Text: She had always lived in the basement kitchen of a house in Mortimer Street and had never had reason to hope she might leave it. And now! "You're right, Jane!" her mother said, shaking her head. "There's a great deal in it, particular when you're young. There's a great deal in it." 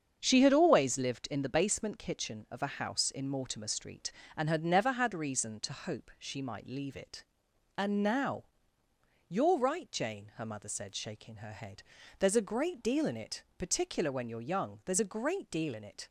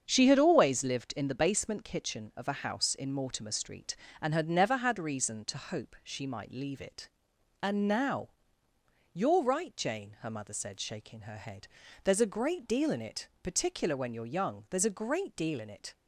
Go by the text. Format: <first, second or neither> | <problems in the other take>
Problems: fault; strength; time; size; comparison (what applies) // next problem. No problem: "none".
neither | starts louder than the rest; strong; the same in both